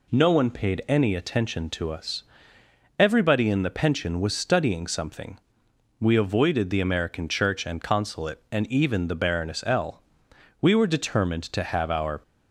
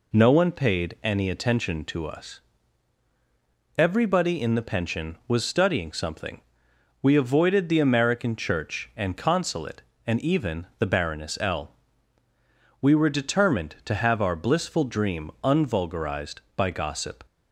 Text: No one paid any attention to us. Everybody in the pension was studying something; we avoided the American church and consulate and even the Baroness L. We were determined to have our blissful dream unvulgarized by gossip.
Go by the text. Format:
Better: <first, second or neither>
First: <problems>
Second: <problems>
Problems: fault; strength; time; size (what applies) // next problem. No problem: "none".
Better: second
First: stops before "blissful dream unvulgarized by gossip"; at 12.2 s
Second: none